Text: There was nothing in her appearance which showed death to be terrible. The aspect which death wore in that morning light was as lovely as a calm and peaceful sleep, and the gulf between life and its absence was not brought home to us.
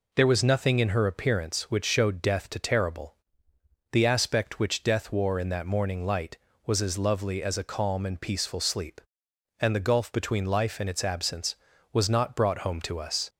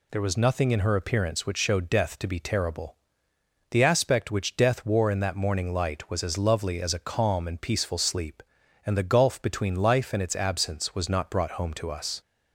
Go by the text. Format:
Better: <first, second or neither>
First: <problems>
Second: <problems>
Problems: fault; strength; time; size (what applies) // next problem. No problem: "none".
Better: second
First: skips "be"; at 2.5 s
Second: none